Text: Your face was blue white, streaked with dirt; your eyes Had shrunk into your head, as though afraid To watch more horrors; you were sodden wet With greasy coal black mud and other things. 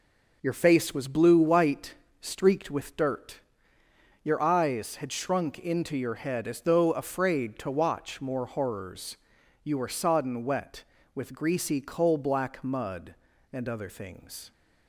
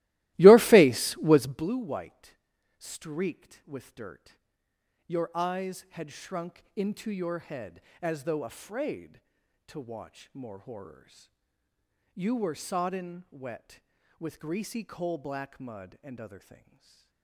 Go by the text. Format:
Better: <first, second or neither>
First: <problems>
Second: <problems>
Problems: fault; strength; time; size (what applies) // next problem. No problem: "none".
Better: first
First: none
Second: starts louder than the rest; strong; until 1.7 s; 17.5 dB // stays silent after the last word; slight; from 16.3 s on; 0.9 s long